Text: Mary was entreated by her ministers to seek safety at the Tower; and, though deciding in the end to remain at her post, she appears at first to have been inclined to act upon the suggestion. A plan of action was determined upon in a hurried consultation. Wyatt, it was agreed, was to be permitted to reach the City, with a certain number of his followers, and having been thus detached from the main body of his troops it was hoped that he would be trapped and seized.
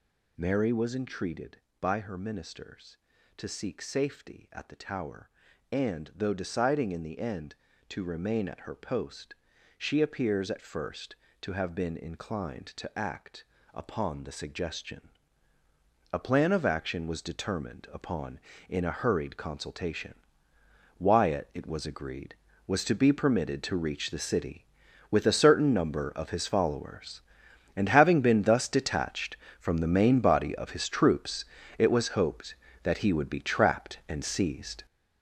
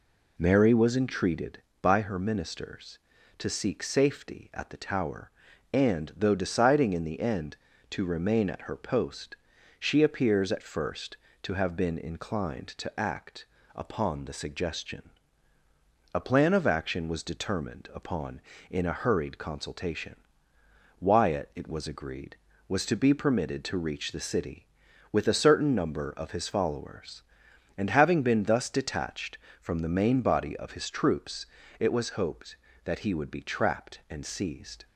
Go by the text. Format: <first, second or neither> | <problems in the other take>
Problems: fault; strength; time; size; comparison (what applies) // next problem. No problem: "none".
second | gets louder; strong; throughout; 9 dB // pauses between "act" and "upon"; slight; at 13.4 s; 0.28 s long; slight in the second // pauses between "troops" and "it"; slight; at 31.4 s; 0.34 s long; slight in the second